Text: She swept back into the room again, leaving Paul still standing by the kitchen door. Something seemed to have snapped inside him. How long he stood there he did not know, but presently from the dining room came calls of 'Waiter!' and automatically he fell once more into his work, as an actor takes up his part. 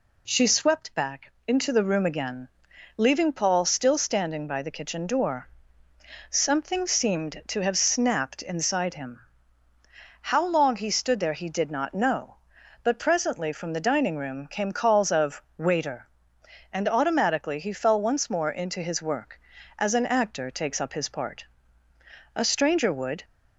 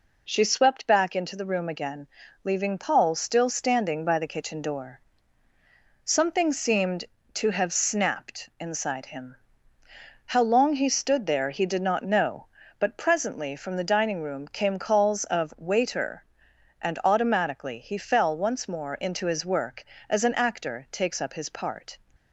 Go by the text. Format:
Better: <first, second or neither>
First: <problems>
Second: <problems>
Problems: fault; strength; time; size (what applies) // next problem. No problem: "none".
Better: second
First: pauses between "back" and "into"; slight; at 1.3 s; 0.16 s long // pauses between "of" and "Waiter"; slight; at 15.4 s; 0.18 s long // goes on to say "A stranger would"; noticeable; from 22.3 s on; 0.88 s long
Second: none